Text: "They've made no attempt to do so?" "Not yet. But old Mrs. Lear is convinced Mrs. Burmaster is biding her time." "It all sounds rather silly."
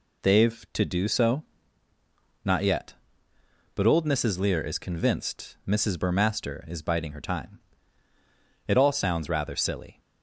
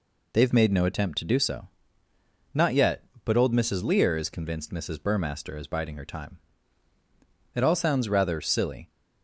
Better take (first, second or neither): second